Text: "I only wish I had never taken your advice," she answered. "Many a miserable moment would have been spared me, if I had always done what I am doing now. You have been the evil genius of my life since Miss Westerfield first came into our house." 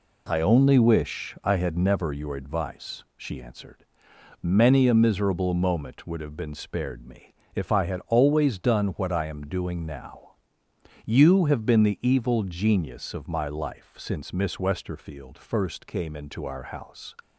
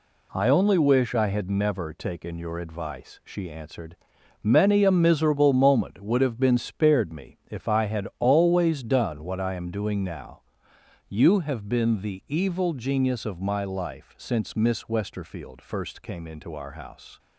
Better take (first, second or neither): second